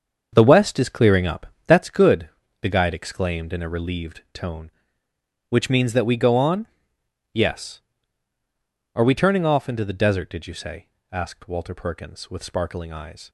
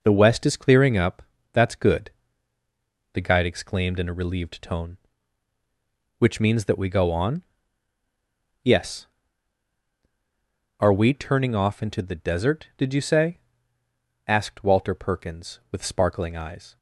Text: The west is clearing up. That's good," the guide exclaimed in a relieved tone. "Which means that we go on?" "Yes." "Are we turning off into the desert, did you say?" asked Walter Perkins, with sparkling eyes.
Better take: second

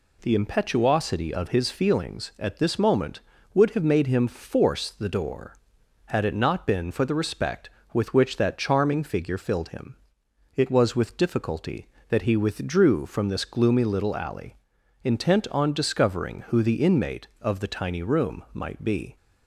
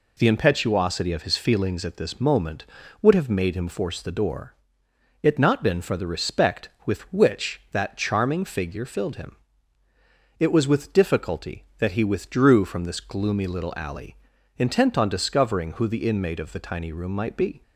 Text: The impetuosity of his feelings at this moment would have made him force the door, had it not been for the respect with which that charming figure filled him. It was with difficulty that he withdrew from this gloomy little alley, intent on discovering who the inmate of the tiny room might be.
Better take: first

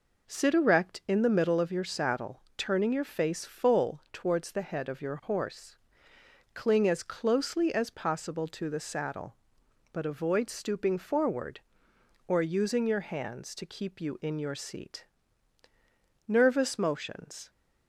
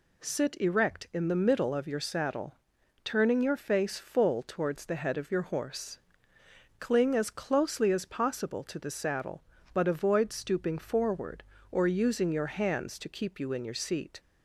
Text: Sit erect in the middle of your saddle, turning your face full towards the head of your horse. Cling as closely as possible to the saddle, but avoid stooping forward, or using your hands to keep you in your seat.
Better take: second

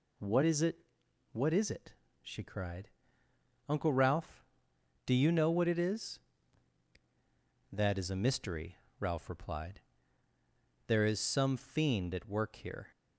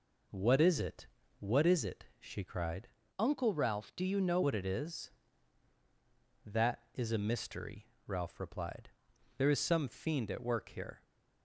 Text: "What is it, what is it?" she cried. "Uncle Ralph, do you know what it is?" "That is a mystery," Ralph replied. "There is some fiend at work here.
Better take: first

